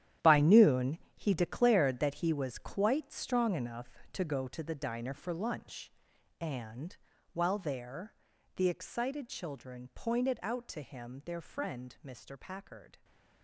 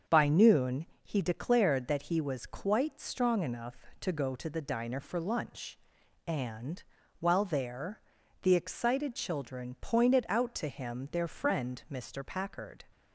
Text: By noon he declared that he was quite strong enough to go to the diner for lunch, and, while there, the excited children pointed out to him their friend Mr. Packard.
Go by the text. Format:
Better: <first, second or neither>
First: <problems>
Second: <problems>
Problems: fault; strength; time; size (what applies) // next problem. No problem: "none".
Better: second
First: gets quieter; strong; throughout; 12 dB // starts louder than the rest; strong; until 1.4 s; 11 dB // pauses between "noon" and "he"; slight; at 0.9 s; 0.18 s long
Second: starts louder than the rest; until 1.2 s; 6.5 dB // pauses between "noon" and "he"; slight; at 0.8 s; 0.18 s long